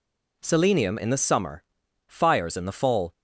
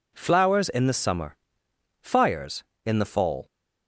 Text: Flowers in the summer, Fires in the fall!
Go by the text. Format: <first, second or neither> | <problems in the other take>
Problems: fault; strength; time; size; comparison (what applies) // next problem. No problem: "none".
second | says "Selenium" for "Flowers"; at 0.4 s